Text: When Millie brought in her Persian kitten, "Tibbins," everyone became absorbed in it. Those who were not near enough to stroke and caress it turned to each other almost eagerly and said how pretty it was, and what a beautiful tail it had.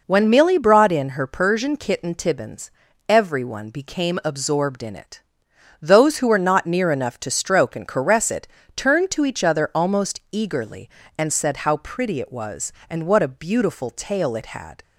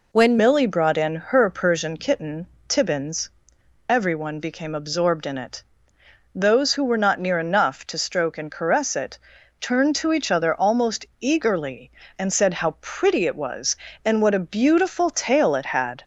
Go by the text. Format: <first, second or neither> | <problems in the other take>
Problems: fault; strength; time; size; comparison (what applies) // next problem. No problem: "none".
first | changes voice at "Millie"; from 0.3 s on; 15.7 s long // pauses between "it" and "turned"; at 9.1 s; 0.44 s long; slight in the first // pauses between "almost" and "eagerly"; slight; at 11.0 s; 0.16 s long